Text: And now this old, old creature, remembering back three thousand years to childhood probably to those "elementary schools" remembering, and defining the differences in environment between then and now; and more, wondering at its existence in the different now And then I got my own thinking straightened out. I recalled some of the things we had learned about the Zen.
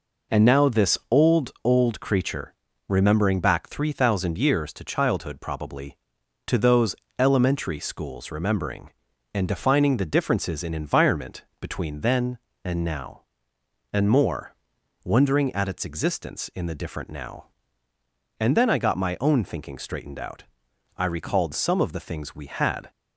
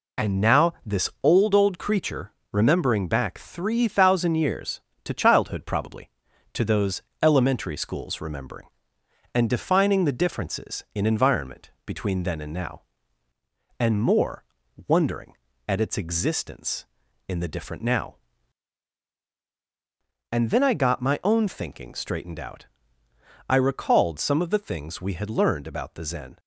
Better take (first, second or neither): second